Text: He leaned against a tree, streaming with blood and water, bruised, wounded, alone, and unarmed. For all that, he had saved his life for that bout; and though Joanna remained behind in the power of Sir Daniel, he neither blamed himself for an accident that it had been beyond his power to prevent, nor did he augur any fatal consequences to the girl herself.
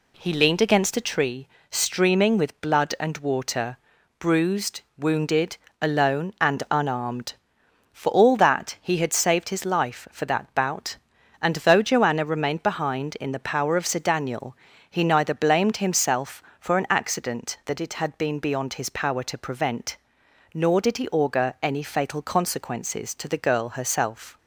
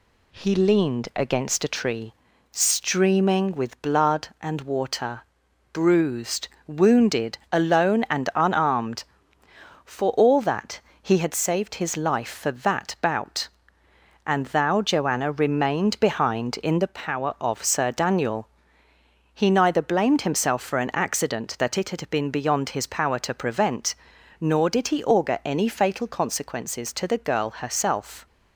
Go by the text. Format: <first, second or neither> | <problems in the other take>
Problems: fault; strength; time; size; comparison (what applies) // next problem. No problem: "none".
first | says "thou" for "though"; at 14.4 s